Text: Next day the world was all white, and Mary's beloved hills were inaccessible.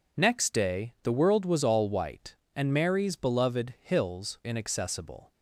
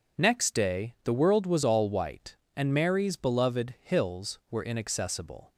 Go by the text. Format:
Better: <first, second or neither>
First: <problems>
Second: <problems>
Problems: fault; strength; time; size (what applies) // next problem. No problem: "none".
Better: second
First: skips "were"; at 4.4 s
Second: none